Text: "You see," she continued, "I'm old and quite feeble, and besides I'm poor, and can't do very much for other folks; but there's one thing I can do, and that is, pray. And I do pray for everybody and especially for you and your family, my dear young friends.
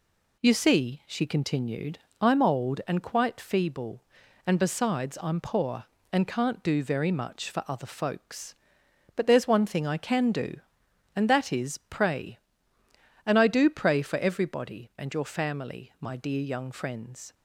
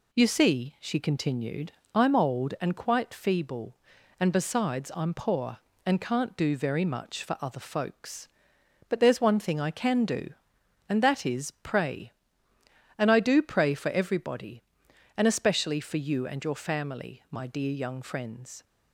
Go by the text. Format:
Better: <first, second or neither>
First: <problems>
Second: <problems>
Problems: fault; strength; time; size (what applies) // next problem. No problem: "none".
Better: second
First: skips "and especially for you"; at 14.9 s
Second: none